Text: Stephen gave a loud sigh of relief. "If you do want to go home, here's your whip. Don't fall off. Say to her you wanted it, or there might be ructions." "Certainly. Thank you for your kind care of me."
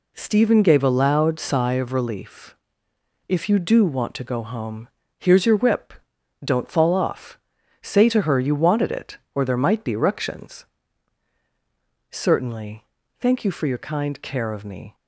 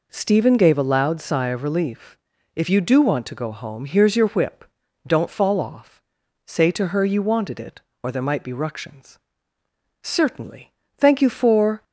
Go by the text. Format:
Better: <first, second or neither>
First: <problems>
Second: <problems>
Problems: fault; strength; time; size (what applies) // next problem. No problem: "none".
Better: first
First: none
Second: stops before "your kind care of me"; at 11.8 s